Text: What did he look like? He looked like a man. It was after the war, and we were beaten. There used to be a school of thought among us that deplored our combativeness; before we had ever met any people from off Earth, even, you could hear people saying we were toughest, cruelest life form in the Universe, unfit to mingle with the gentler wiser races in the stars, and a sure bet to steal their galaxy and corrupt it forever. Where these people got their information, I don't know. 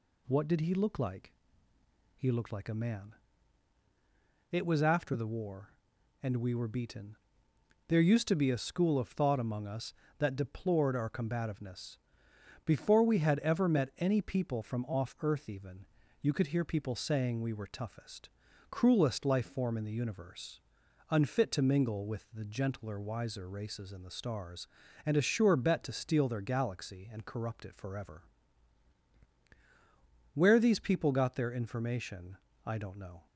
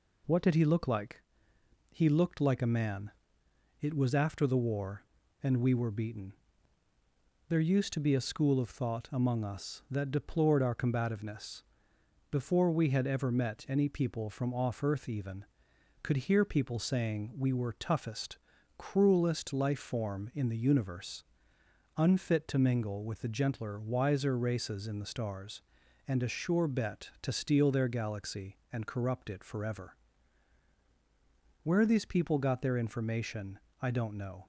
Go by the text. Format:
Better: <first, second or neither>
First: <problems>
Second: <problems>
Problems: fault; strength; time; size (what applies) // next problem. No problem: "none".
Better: first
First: none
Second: skips "you"; at 15.7 s